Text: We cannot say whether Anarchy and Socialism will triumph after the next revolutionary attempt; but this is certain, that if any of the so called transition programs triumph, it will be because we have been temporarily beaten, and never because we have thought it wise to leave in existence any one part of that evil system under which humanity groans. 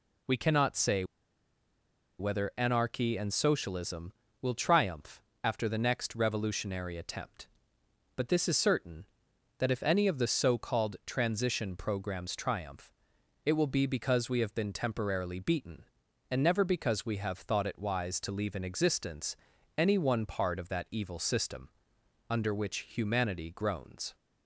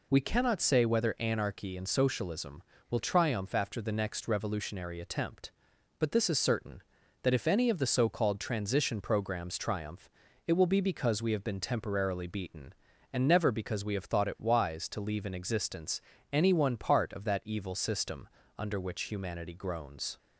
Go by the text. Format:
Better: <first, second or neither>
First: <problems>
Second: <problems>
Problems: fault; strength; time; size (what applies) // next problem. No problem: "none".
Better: second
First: pauses between "say" and "whether"; at 1.0 s; 1.1 s long // pauses between "triumph" and "after"; slight; at 5.2 s; 0.24 s long // pauses between "existence" and "any"; at 19.3 s; 0.40 s long // pauses between "system" and "under"; noticeable; at 21.6 s; 0.62 s long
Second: pauses between "existence" and "any"; slight; at 16.0 s; 0.28 s long // pauses between "system" and "under"; slight; at 18.2 s; 0.32 s long